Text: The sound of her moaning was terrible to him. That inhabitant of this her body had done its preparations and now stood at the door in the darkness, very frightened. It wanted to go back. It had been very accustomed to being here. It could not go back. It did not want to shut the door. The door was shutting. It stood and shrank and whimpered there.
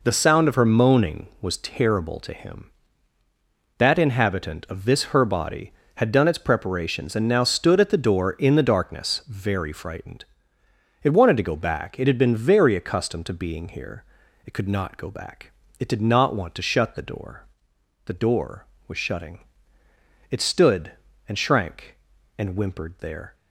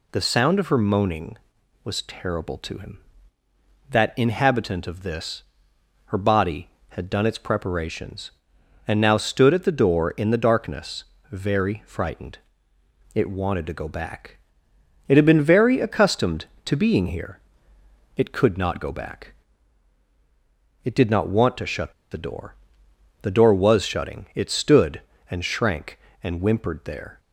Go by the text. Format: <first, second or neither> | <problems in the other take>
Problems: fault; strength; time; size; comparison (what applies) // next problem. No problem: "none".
first | pauses between "this" and "her"; noticeable; at 5.4 s; 0.64 s long // pauses between "shut" and "the"; slight; at 21.9 s; 0.19 s long